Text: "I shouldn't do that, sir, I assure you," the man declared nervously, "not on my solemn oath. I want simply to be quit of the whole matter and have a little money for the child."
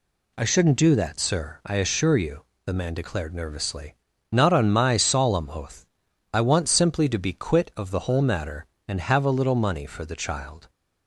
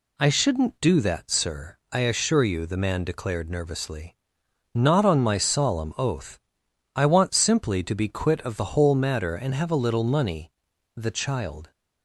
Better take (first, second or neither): first